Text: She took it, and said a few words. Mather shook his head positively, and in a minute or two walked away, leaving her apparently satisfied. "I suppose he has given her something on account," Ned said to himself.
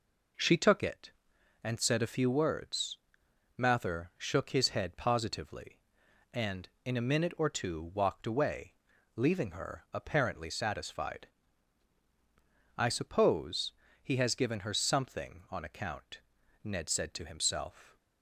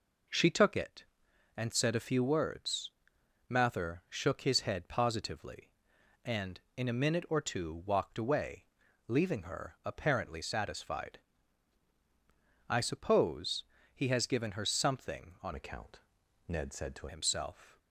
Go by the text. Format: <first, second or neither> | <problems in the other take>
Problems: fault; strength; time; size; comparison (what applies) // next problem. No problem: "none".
first | pauses between "suppose" and "he"; slight; at 13.6 s; 0.30 s long; slight in the first // changes voice from "account" to "to"; from 15.5 to 17.0 s; 1.5 s long